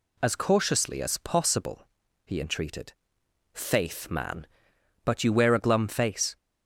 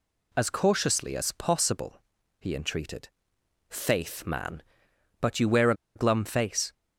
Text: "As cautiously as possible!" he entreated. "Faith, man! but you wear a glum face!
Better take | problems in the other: first | pauses between "a" and "glum"; slight; at 5.7 s; 0.21 s long

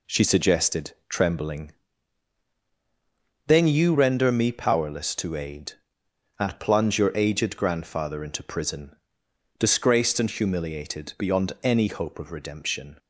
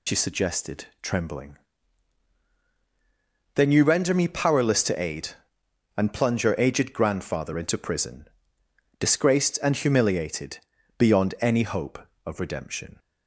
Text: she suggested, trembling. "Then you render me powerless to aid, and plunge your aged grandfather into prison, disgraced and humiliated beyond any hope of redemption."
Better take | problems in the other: first | loses the start of "she"; at 0.0 s; 75 ms // pauses between "humiliated" and "beyond"; at 10.5 s; 0.40 s long

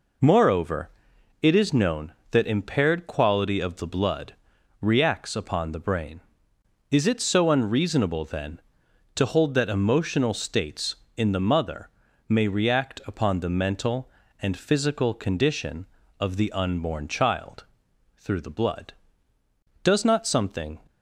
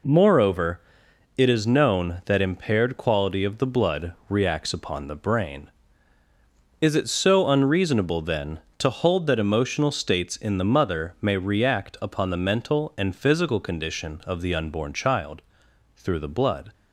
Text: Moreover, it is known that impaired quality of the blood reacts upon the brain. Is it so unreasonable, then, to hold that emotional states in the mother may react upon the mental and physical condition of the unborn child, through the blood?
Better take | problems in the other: second | pauses between "blood" and "reacts"; noticeable; at 4.3 s; 0.48 s long; slight in the second // pauses between "mother" and "may"; at 11.8 s; 0.40 s long // goes on to say "Does not something"; noticeable; from 19.8 s on; 0.96 s long

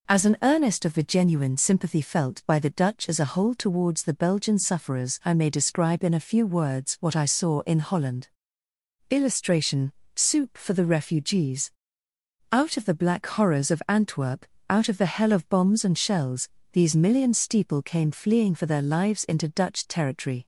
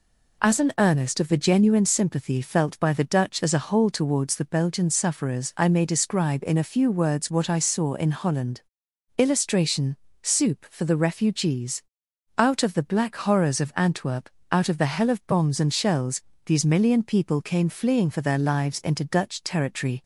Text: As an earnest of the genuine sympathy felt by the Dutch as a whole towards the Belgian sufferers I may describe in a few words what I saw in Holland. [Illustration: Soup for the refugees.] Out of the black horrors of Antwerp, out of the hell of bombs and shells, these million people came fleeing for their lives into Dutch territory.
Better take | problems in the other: second | says "steeple" for "people"; at 17.3 s

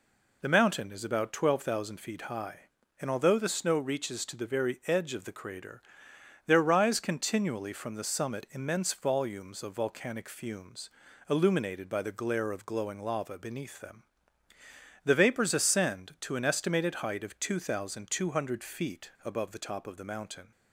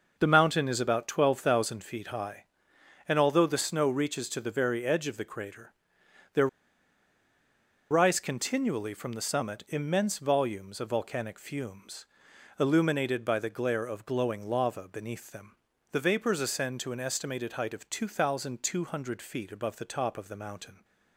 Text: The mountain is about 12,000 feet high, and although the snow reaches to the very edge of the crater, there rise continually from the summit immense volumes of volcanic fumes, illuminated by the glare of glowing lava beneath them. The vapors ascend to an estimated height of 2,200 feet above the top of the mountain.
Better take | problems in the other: first | pauses between "there" and "rise"; strong; at 6.4 s; 1.4 s long

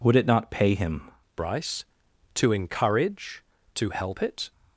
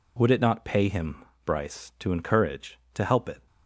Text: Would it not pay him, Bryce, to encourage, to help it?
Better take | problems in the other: second | changes voice at "Bryce"; from 1.3 s on; 3.2 s long

